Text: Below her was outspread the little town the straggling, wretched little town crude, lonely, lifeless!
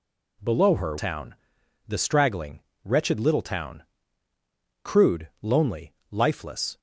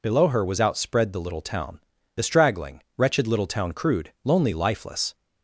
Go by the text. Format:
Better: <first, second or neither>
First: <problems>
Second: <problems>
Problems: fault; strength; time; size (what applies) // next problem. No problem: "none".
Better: second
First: skips "was outspread the little"; at 0.9 s // pauses between "town" and "the"; noticeable; at 1.3 s; 0.54 s long // pauses between "town" and "crude"; at 3.8 s; 1.0 s long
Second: pauses between "town" and "the"; at 1.7 s; 0.38 s long